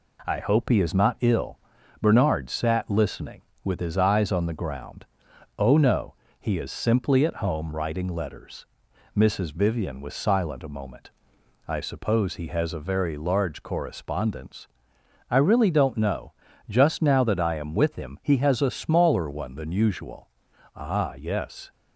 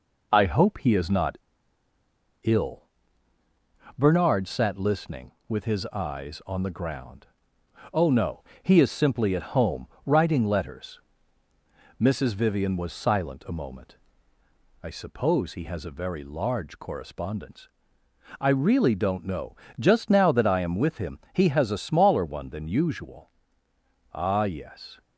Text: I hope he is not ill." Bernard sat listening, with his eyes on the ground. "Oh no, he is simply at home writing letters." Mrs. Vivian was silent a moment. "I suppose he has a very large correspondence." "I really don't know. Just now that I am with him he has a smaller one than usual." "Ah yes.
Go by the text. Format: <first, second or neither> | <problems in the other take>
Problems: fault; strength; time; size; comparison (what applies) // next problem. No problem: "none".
first | pauses between "not" and "ill"; at 1.3 s; 1.0 s long // pauses between "home" and "writing"; slight; at 9.8 s; 0.18 s long